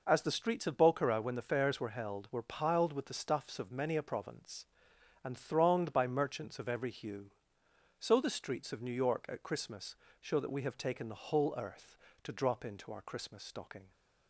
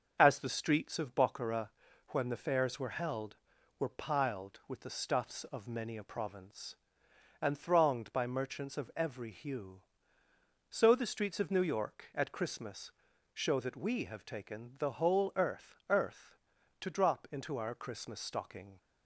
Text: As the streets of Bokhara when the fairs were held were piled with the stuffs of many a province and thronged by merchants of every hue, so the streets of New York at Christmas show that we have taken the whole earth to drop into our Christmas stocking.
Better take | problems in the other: first | starts louder than the rest; until 1.2 s; 6.5 dB // pauses between "Bokhara" and "when"; at 1.6 s; 0.40 s long // pauses between "Christmas" and "show"; at 12.9 s; 0.42 s long; slight in the first // says "earth" twice; at 15.8 s

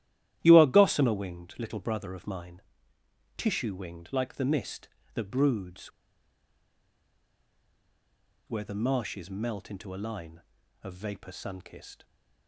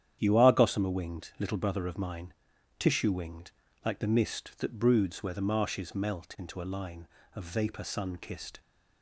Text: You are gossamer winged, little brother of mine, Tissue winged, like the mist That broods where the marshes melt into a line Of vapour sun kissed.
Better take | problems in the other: second | starts louder than the rest; strong; until 1.4 s; 13.5 dB; strong in the second // pauses between "broods" and "where"; strong; at 5.8 s; 2.5 s long

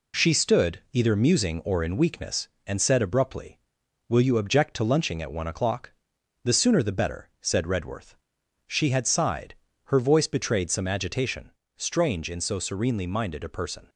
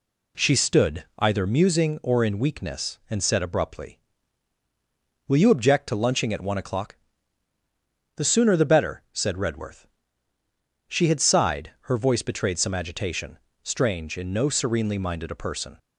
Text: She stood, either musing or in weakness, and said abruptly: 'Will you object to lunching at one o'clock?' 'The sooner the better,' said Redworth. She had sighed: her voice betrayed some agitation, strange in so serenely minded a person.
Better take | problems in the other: first | says "no" for "so"; at 14.3 s

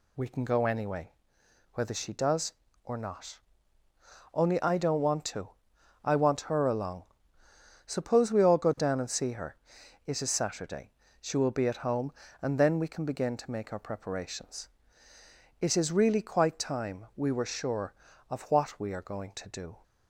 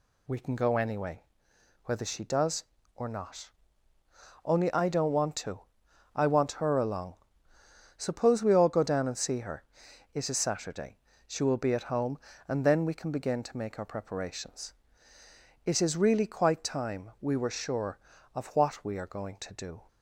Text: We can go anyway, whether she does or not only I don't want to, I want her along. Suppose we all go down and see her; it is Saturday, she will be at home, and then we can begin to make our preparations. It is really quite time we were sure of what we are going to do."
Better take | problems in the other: neither | pauses between "not" and "only"; noticeable; the same in both

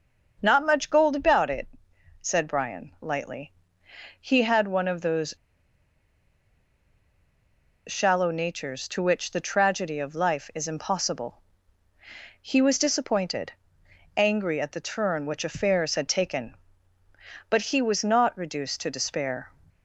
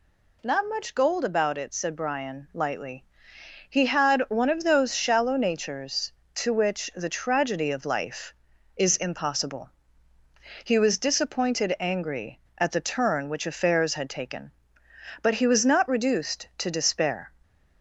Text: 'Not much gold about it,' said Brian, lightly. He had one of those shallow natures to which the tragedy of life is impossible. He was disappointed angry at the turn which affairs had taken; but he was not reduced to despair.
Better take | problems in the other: second | starts louder than the rest; until 1.4 s; 6 dB // pauses between "those" and "shallow"; strong; at 5.3 s; 2.5 s long // pauses between "disappointed" and "angry"; noticeable; at 13.5 s; 0.64 s long

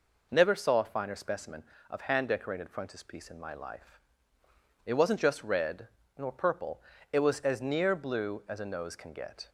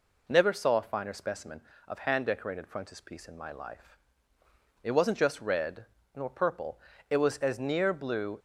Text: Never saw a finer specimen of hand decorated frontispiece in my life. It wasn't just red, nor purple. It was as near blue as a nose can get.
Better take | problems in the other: first | stops before "as a nose can get"; at 8.3 s

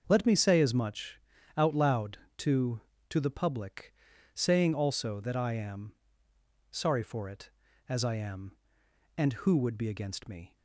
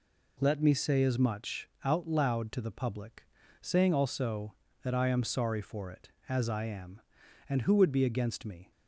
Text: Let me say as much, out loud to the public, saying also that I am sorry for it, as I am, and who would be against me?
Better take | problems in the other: second | starts louder than the rest; noticeable; until 1.0 s; 6 dB // says "to" twice; at 3.0 s // pauses between "am" and "sorry"; noticeable; at 5.9 s; 0.78 s long

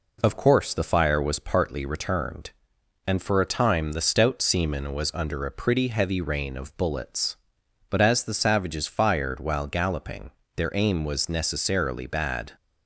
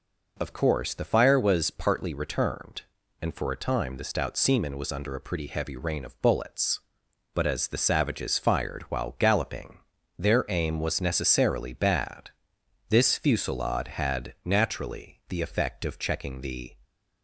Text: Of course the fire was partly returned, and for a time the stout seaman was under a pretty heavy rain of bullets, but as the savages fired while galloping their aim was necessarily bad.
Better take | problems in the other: first | pauses between "galloping" and "their"; at 9.7 s; 0.42 s long; slight in the first // goes on to say "This fusillade had naturally the effect of checking the"; strong; from 12.8 s on; 3.8 s long

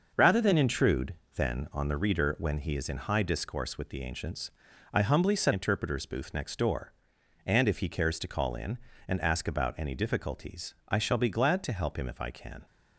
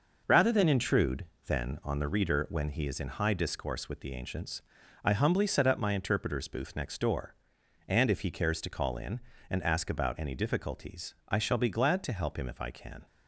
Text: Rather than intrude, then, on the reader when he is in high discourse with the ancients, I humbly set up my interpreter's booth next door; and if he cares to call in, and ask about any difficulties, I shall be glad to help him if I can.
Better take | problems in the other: second | skips "up my"; at 5.5 s

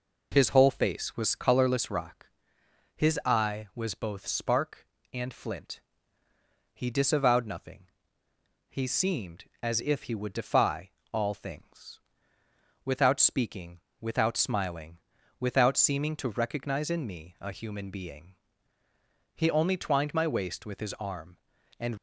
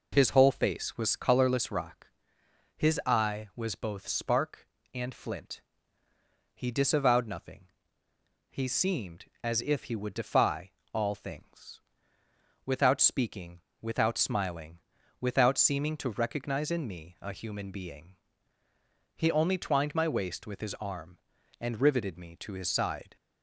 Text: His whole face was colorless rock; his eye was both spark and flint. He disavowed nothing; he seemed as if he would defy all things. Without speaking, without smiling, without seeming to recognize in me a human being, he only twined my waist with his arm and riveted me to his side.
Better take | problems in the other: second | pauses between "defy" and "all"; slight; at 10.8 s; 0.22 s long; slight in the second // stops before "riveted me to his side"; at 21.9 s

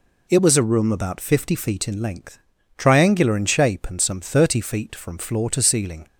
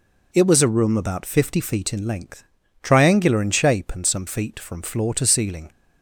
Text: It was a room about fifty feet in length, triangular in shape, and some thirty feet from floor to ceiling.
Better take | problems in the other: first | skips "thirty"; at 4.2 s

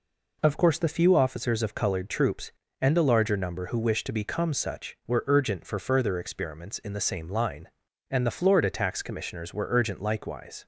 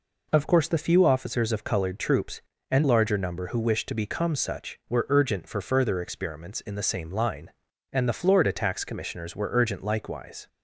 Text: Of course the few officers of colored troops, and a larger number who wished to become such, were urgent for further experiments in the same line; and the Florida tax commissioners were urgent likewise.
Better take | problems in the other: first | skips "a"; at 2.8 s

